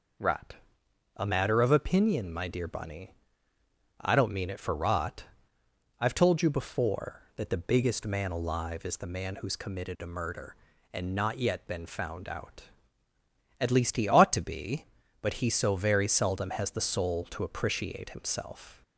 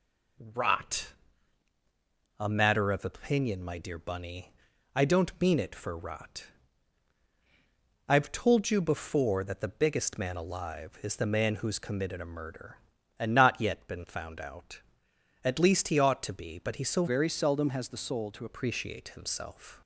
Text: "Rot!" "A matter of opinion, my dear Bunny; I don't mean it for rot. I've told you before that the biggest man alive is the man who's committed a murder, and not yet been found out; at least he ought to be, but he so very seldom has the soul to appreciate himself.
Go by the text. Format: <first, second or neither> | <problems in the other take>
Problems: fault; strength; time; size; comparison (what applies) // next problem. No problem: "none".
first | changes voice from "very" to "to"; from 17.0 to 18.4 s; 1.4 s long